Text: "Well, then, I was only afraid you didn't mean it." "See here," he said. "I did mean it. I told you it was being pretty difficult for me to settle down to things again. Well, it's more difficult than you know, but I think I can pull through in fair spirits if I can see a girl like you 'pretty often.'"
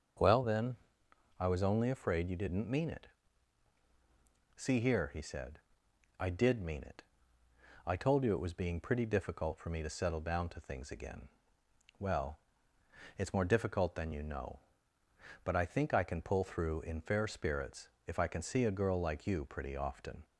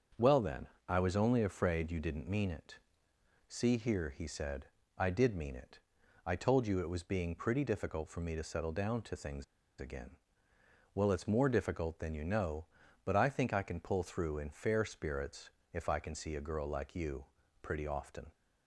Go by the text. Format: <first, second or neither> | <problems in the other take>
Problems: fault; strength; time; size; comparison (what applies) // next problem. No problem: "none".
first | starts louder than the rest; until 1.4 s; 7 dB; also in the first // pauses between "things" and "again"; slight; at 9.4 s; 0.36 s long // pauses between "spirits" and "if"; slight; at 15.5 s; 0.22 s long; slight in the first // pauses between "you" and "pretty"; slight; at 17.2 s; 0.36 s long